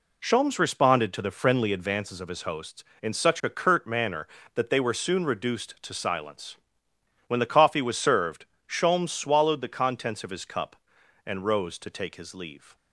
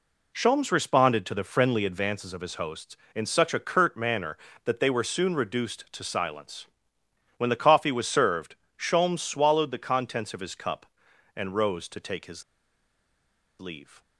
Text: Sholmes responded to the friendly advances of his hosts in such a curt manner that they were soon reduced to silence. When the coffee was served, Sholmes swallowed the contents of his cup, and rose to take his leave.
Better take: first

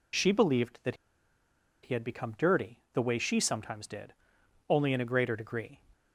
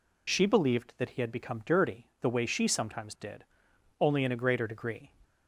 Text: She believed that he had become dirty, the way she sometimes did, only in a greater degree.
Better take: second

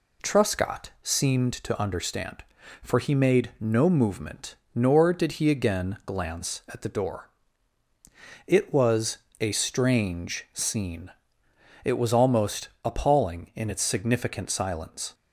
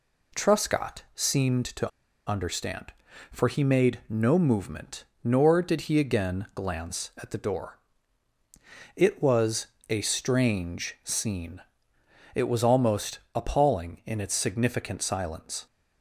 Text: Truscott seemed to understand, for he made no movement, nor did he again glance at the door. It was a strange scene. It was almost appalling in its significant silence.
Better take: first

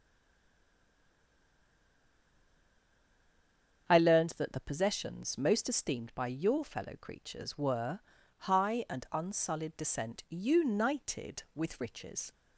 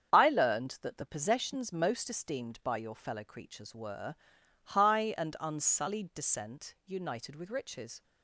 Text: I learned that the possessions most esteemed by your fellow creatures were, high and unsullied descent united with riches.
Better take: second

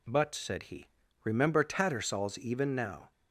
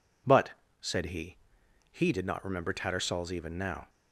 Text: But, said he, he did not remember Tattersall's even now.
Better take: second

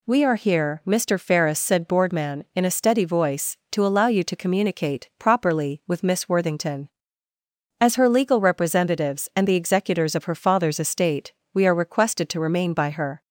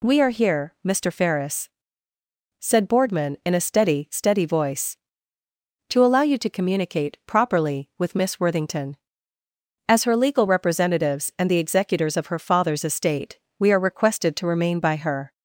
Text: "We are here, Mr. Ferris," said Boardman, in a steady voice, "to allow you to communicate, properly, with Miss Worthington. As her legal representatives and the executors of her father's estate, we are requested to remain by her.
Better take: first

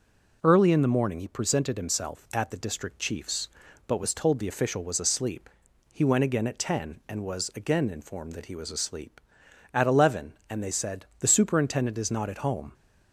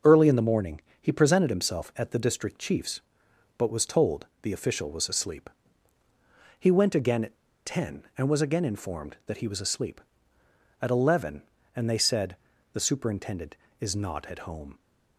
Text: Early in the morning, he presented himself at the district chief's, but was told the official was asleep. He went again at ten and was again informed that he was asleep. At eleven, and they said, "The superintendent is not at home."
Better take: first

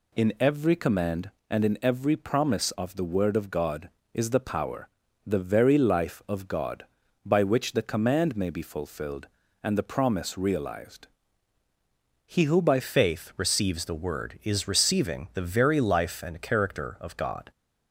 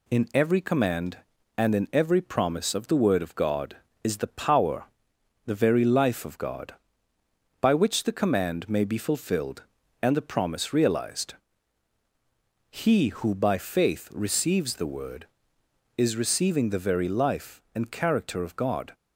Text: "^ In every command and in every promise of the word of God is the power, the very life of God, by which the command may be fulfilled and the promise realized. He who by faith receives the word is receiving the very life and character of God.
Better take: second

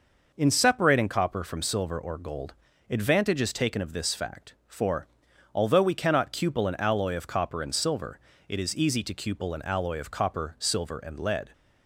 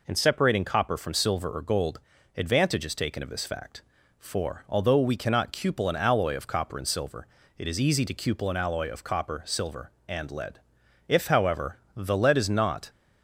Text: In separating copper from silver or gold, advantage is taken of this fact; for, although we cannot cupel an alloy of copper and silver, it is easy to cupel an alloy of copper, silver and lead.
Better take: first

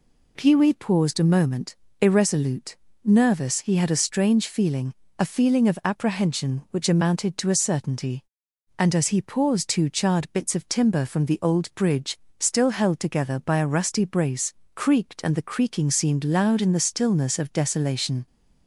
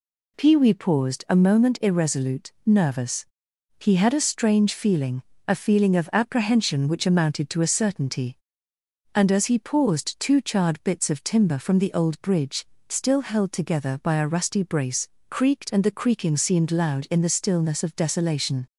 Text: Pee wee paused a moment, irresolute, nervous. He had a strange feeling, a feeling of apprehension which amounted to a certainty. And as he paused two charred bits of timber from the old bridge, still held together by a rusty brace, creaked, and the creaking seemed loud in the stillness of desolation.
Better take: neither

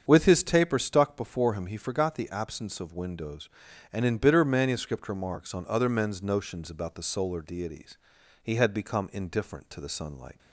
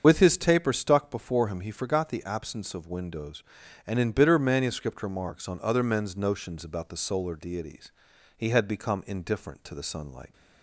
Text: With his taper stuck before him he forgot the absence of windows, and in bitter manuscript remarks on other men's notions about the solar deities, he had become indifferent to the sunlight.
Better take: first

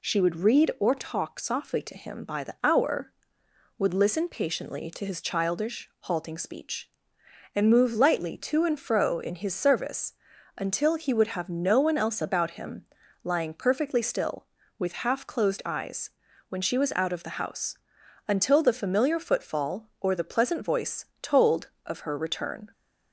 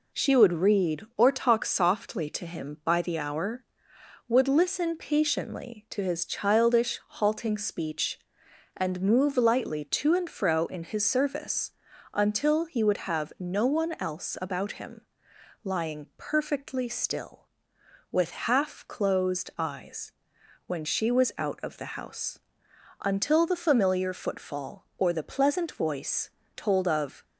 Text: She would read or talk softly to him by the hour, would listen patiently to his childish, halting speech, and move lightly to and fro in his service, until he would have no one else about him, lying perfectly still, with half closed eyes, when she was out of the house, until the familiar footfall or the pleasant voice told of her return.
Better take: first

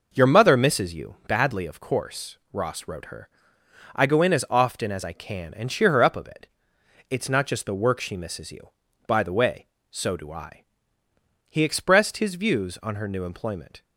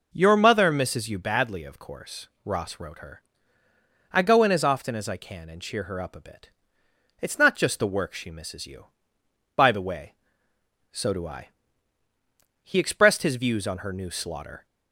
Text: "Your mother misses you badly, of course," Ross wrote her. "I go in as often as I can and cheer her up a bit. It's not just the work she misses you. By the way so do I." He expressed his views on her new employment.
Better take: first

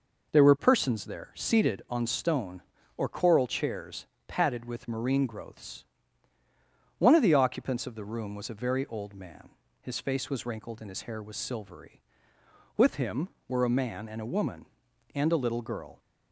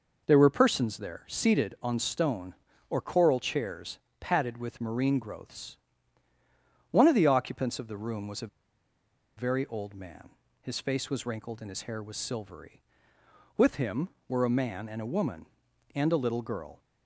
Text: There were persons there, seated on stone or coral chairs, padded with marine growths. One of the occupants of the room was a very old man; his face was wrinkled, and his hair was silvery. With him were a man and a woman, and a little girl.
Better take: first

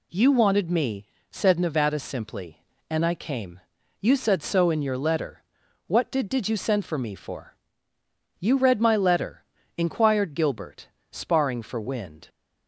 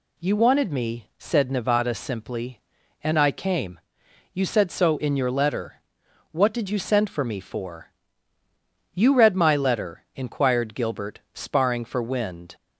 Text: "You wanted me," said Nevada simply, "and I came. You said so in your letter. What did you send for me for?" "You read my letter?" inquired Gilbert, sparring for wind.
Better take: second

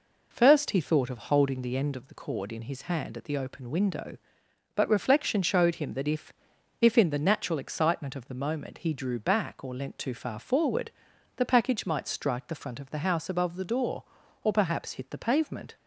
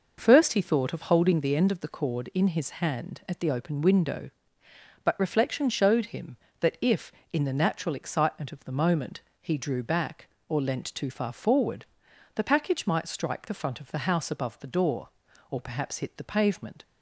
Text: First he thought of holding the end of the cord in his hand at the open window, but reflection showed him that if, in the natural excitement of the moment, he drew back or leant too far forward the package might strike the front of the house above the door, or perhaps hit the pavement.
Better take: second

